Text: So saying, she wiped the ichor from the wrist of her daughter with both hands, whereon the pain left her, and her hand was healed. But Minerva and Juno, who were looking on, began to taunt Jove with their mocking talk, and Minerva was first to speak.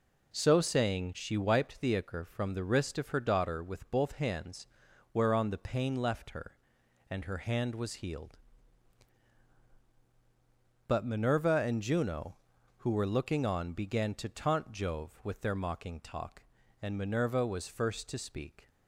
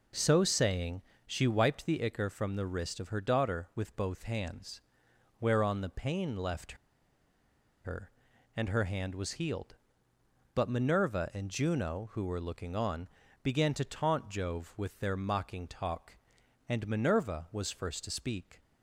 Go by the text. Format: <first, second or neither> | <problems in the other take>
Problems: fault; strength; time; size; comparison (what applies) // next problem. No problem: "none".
first | pauses between "left" and "her"; at 6.7 s; 1.0 s long